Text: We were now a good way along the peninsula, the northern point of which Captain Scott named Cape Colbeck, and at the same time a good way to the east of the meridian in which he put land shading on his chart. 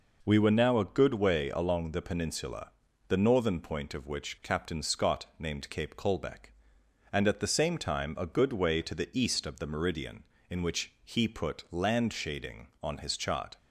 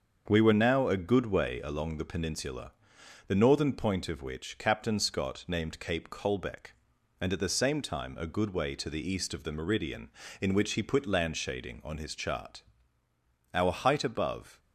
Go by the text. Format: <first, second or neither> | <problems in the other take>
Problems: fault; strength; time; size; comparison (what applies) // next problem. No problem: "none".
first | starts louder than the rest; until 1.2 s; 6.5 dB // goes on to say "Our height above"; noticeable; from 13.5 s on; 1.0 s long